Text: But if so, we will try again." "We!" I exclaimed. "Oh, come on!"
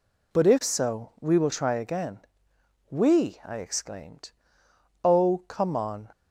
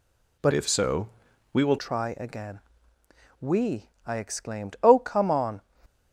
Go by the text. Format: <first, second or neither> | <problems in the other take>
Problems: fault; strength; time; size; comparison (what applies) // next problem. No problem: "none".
first | changes voice from "if" to "will"; from 0.5 to 1.7 s; 1.2 s long